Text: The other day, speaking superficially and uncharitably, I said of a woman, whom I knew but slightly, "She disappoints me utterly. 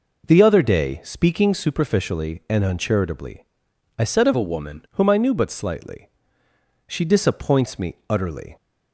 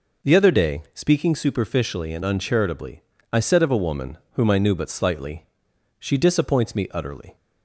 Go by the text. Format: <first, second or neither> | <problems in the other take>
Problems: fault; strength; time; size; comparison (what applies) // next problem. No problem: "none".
second | changes voice from "a" to "woman"; from 4.3 to 4.8 s; 0.5 s long